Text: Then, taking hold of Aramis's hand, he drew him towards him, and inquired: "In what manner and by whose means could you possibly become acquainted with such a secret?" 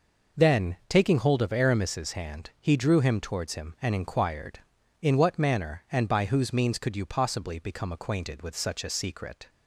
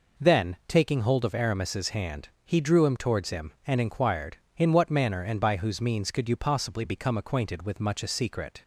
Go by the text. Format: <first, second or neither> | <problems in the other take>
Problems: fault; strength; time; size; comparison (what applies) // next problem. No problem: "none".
first | says "much" for "such"; at 7.7 s